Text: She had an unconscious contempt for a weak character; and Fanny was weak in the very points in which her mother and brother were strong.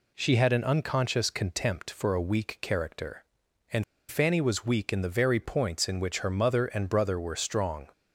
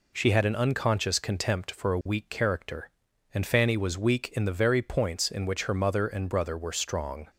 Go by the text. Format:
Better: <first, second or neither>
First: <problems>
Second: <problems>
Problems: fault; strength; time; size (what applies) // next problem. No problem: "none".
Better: second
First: pauses between "and" and "Fanny"; slight; at 3.8 s; 0.25 s long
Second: none